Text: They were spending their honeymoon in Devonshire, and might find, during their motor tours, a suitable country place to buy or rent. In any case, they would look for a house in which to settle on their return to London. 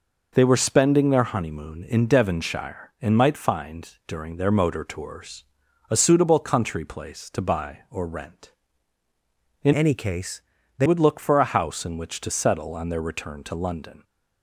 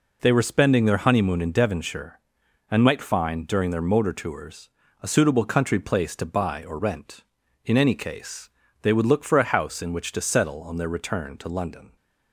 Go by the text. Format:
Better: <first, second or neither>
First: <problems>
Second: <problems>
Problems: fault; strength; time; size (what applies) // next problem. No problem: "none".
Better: second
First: changes voice from "any" to "they"; from 9.7 to 10.8 s; 1.1 s long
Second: none